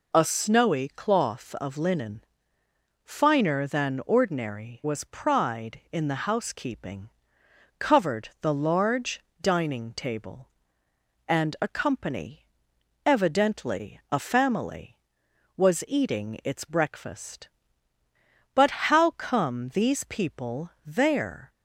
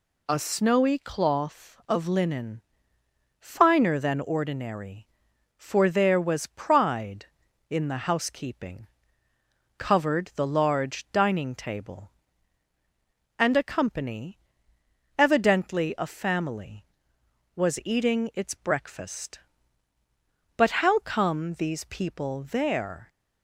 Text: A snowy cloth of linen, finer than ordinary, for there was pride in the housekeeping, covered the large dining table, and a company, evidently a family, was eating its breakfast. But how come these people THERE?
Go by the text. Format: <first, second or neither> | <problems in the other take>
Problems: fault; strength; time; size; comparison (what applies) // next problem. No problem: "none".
second | skips "for there"; at 4.8 s // pauses between "large" and "dining"; slight; at 9.1 s; 0.22 s long // pauses between "people" and "THERE"; slight; at 20.7 s; 0.16 s long